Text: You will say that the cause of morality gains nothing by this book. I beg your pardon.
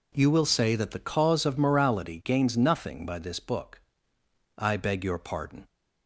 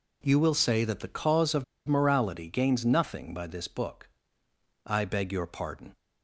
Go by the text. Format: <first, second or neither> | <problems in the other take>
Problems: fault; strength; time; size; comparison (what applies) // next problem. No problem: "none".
first | pauses between "of" and "morality"; slight; at 1.6 s; 0.23 s long